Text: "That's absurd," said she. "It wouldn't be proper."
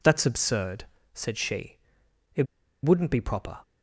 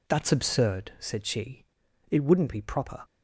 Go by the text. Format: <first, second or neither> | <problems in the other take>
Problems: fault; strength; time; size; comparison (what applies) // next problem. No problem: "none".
second | pauses between "It" and "wouldn't"; at 2.4 s; 0.40 s long